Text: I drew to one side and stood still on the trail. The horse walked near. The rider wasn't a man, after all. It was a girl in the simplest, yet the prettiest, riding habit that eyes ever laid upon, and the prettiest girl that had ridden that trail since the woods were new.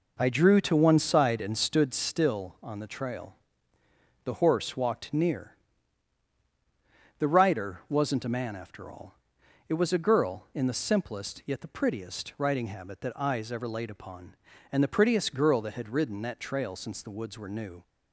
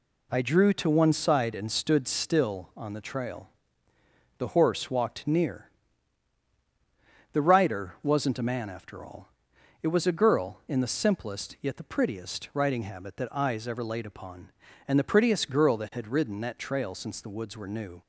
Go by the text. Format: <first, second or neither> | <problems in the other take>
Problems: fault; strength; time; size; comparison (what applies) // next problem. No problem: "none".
second | starts louder than the rest; noticeable; until 1.9 s; 5 dB